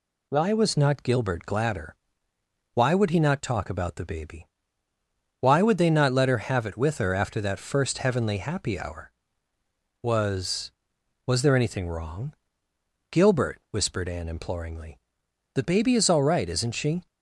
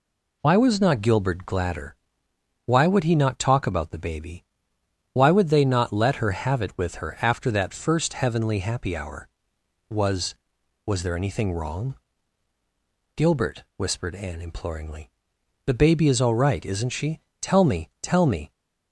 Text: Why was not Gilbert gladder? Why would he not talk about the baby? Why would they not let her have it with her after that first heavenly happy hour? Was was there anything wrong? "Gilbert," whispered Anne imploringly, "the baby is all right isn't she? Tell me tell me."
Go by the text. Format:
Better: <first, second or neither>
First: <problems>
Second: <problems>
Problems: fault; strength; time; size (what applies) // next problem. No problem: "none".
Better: second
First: stops before "Tell me tell me"; at 17.0 s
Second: none